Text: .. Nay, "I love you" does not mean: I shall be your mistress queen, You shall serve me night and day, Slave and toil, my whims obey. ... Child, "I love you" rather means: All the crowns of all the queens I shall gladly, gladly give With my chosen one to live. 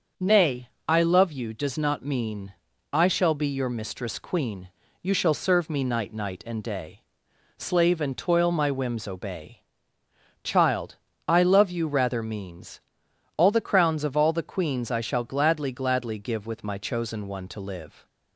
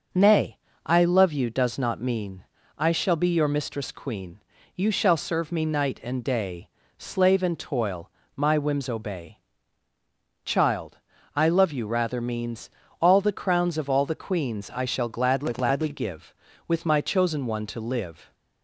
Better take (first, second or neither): second